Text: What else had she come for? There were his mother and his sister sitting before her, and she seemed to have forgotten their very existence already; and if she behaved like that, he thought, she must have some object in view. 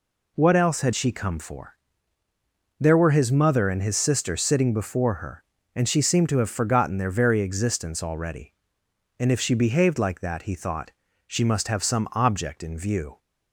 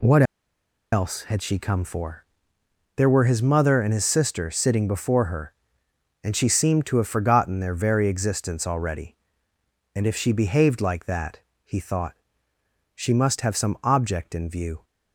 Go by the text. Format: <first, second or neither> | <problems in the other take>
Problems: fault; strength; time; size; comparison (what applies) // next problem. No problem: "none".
first | pauses between "What" and "else"; noticeable; at 0.2 s; 0.69 s long